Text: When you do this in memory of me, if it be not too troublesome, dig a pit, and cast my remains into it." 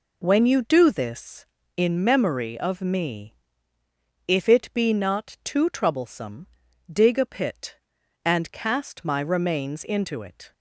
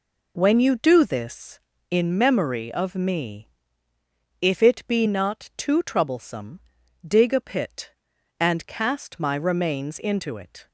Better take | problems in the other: neither | none

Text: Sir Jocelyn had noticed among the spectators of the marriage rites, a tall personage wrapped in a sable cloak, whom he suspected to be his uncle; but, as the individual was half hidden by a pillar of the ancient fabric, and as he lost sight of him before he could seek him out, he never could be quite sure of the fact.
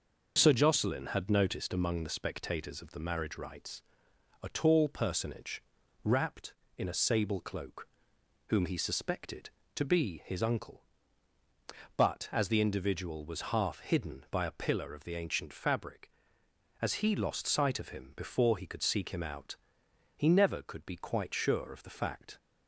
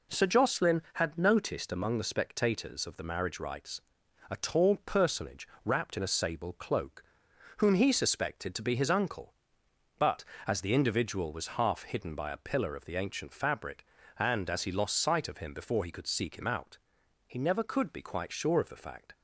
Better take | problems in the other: second | pauses between "personage" and "wrapped"; at 5.6 s; 0.40 s long; slight in the second // skips "and"; at 16.4 s

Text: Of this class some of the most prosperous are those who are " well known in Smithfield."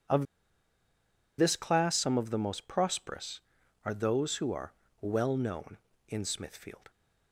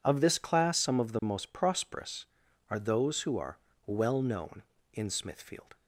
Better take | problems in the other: second | pauses between "Of" and "this"; at 0.2 s; 1.1 s long

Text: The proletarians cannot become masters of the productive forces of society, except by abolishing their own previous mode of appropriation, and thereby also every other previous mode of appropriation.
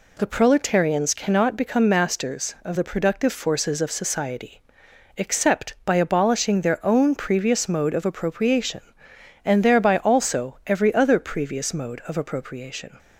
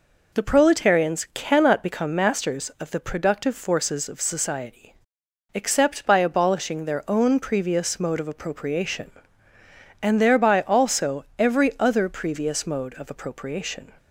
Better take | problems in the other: neither | none

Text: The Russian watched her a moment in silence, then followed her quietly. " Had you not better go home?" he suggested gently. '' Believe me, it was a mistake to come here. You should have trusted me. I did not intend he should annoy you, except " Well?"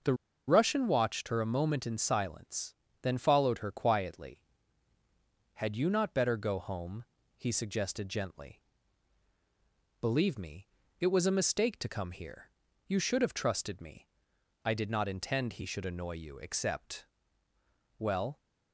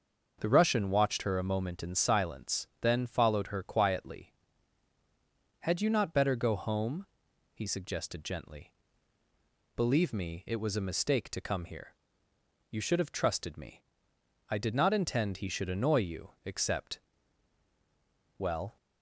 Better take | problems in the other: second | starts louder than the rest; strong; until 1.3 s; 7.5 dB; also in the second // pauses between "The" and "Russian"; slight; at 0.1 s; 0.34 s long

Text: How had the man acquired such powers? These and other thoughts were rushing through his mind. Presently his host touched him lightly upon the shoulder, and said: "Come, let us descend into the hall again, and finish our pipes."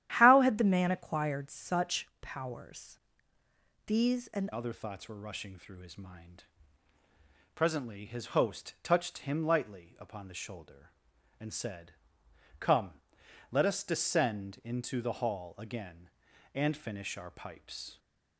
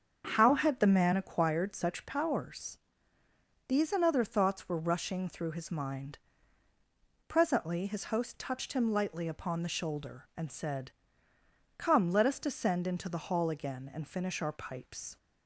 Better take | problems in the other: second | starts louder than the rest; strong; until 1.1 s; 11.5 dB; strong in the second // changes voice at "other"; from 4.5 s on; 13.4 s long

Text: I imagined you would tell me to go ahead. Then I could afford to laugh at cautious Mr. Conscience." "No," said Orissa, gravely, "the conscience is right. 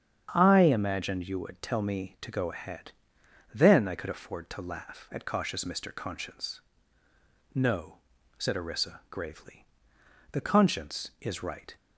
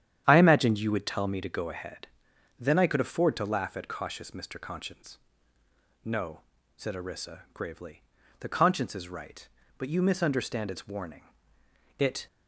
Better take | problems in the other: first | starts louder than the rest; strong; until 1.2 s; 10 dB; strong in the first // goes on to say "But you misunderstand its warning It"; strong; from 9.7 s on; 2.4 s long

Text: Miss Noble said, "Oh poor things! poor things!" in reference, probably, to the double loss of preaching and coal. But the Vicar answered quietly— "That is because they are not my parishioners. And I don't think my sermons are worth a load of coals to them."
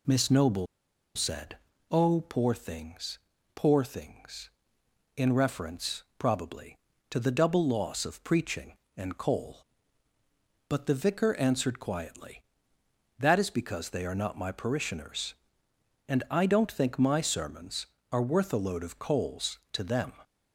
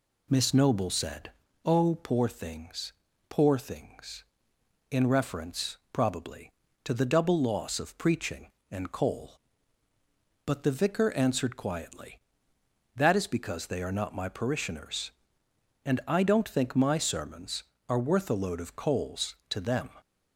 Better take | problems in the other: second | pauses between "Noble" and "said"; noticeable; at 0.6 s; 0.50 s long

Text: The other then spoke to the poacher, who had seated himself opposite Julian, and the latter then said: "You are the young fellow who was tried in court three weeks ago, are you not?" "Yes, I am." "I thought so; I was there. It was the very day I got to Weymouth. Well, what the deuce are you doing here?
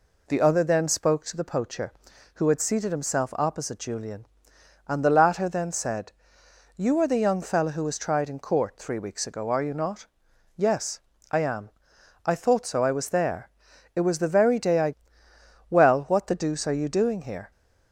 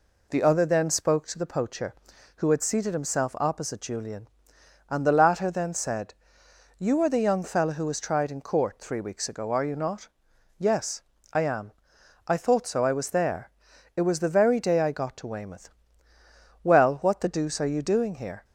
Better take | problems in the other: second | skips "got to Weymouth"; at 15.2 s

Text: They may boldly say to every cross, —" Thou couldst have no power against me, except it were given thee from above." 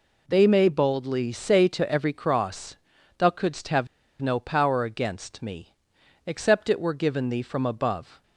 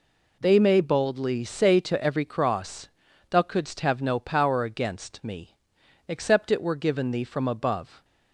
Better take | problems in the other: second | pauses between "have" and "no"; slight; at 3.8 s; 0.35 s long

